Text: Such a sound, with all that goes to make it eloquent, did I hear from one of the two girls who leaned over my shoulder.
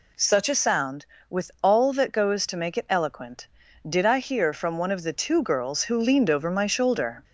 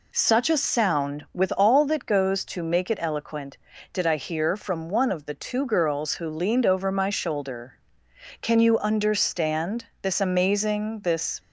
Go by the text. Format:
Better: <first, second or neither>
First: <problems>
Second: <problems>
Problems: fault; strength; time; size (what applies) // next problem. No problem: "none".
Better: first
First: none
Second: goes on to say "Can you understand this amazing this"; strong; from 8.4 s on; 2.9 s long